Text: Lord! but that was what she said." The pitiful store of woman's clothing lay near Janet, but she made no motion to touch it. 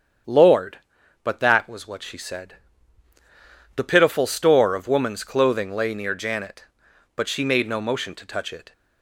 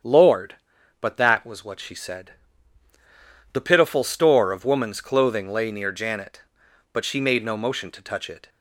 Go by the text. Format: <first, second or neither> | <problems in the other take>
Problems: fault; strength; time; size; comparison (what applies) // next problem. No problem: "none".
neither | starts louder than the rest; strong; the same in both